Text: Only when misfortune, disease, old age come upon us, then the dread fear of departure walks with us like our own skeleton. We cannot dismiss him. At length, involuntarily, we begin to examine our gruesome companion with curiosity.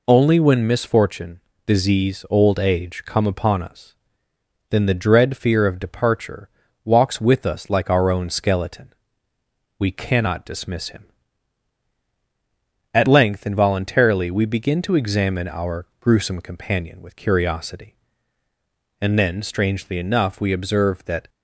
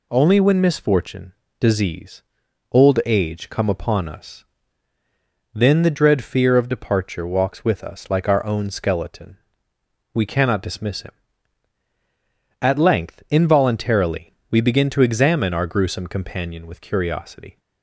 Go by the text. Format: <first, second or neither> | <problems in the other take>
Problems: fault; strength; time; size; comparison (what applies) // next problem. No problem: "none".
second | pauses between "departure" and "walks"; slight; at 6.4 s; 0.34 s long // goes on to say "And then strangely enough we observe that"; strong; from 19.0 s on; 2.2 s long